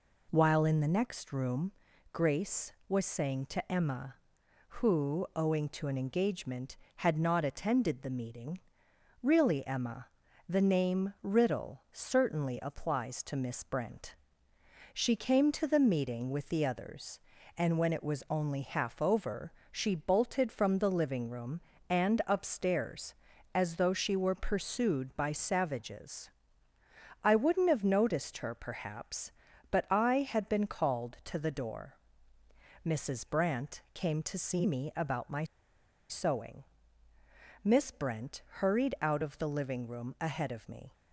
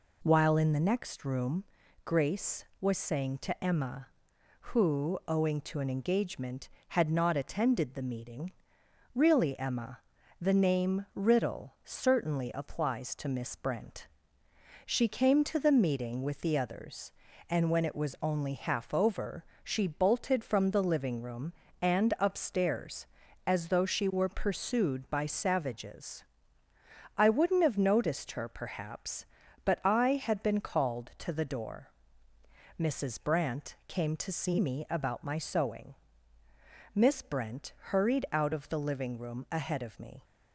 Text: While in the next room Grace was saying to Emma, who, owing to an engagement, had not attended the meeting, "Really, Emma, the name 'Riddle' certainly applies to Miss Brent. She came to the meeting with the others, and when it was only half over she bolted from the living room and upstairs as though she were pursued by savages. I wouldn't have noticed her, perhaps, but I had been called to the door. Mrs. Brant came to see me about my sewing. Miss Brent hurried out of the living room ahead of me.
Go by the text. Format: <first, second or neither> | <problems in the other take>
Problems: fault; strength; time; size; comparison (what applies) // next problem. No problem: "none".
second | pauses between "room" and "Grace"; at 1.7 s; 0.40 s long; also in the second // pauses between "over" and "she"; slight; at 19.5 s; 0.20 s long; slight in the second // pauses between "my" and "sewing"; noticeable; at 35.4 s; 0.66 s long